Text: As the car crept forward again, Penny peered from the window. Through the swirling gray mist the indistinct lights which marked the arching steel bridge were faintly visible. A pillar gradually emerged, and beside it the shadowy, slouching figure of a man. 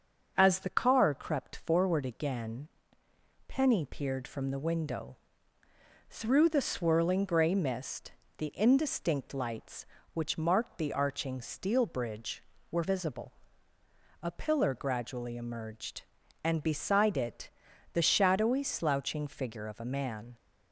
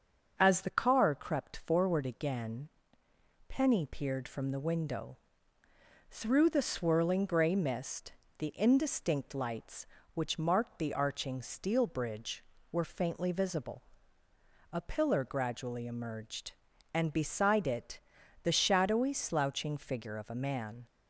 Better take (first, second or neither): second